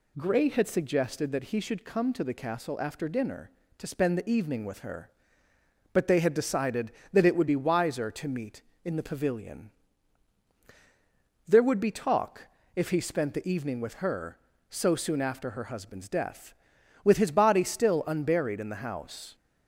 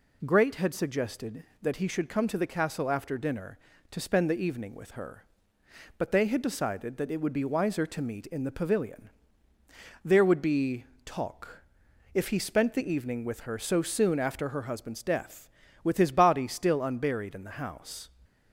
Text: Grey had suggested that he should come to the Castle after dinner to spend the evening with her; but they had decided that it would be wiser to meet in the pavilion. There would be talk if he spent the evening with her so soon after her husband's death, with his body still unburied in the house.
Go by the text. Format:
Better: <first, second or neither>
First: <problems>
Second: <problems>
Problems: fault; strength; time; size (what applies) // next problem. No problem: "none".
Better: first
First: pauses between "talk" and "if"; slight; at 12.4 s; 0.28 s long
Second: says "Great" for "Grey"; at 0.2 s // pauses between "be" and "talk"; slight; at 10.8 s; 0.20 s long // pauses between "talk" and "if"; noticeable; at 11.6 s; 0.50 s long